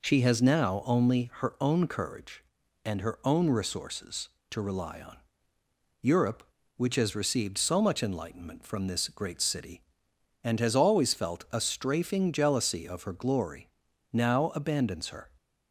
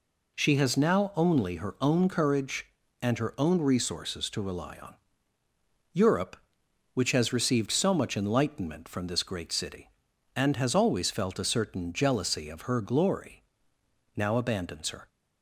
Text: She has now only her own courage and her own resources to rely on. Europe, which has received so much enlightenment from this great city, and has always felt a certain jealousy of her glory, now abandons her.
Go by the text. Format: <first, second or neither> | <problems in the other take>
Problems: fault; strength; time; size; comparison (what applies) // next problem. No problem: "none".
second | says "strafing" for "certain"; at 11.6 s